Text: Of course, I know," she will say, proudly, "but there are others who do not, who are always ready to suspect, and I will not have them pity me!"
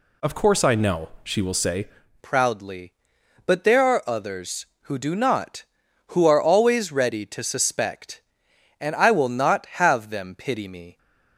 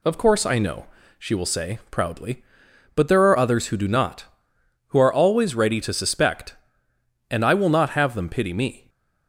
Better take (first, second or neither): second